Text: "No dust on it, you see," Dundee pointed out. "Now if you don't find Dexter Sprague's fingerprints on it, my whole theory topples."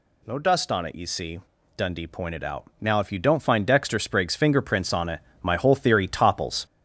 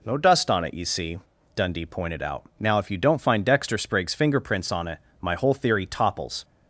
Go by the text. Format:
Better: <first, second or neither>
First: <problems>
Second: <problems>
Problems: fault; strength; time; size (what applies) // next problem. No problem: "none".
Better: second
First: gets louder; noticeable; throughout; 5 dB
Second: none